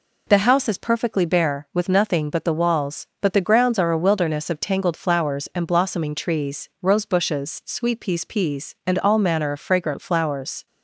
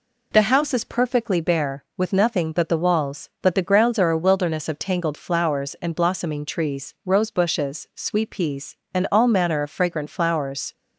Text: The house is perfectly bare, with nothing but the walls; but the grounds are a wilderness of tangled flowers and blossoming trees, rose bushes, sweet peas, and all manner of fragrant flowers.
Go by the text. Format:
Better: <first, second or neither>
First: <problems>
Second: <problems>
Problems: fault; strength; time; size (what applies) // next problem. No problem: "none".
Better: second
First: says "peas" twice; at 8.2 s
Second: none